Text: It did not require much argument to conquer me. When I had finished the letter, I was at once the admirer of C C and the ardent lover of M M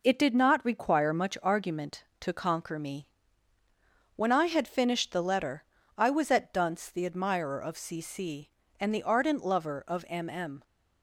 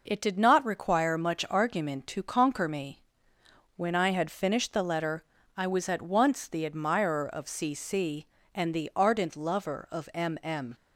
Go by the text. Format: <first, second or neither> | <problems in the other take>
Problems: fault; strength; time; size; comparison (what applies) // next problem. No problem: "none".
second | says "dunce" for "once"; at 6.5 s